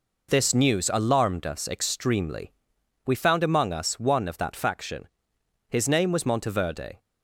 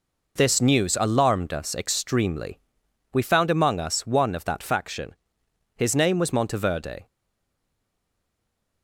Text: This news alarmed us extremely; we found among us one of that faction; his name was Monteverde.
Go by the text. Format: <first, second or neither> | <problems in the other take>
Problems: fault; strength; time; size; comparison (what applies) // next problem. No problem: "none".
first | stays silent after the last word; noticeable; from 7.0 s on; 1.8 s long